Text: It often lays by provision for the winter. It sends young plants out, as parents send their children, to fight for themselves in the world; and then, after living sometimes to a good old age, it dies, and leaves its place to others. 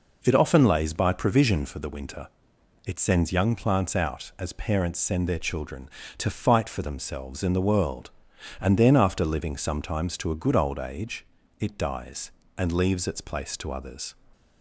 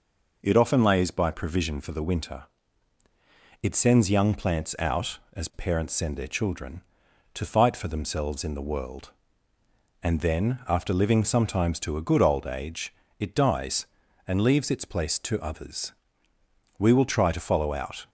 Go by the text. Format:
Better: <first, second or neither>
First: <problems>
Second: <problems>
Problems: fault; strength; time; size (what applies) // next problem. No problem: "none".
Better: first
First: none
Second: goes on to say "We will try to follow out"; noticeable; from 16.7 s on; 1.3 s long